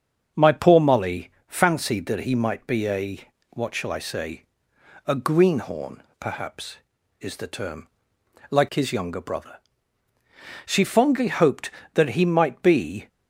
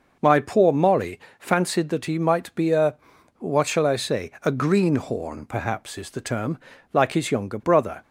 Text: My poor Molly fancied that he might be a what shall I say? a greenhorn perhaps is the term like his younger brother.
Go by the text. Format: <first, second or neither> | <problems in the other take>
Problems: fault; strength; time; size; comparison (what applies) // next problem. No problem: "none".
second | starts louder than the rest; until 1.5 s; 6.5 dB // pauses between "Molly" and "fancied"; slight; at 1.2 s; 0.18 s long; slight in the second // pauses between "a" and "what"; slight; at 3.1 s; 0.32 s long; also in the second // pauses between "greenhorn" and "perhaps"; slight; at 6.0 s; 0.18 s long // pauses between "term" and "like"; noticeable; at 7.8 s; 0.64 s long; slight in the second // goes on to say "She fondly hoped that he might be"; strong; from 10.6 s on; 2.4 s long